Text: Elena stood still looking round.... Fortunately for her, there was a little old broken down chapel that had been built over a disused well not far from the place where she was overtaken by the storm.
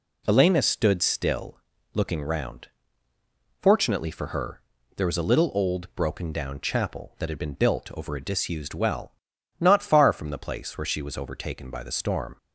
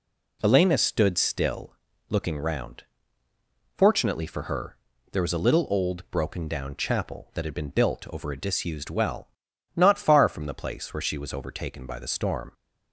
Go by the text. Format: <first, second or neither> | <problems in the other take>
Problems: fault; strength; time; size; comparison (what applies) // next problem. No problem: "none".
neither | pauses between "still" and "looking"; slight; the same in both // pauses between "well" and "not"; noticeable; the same in both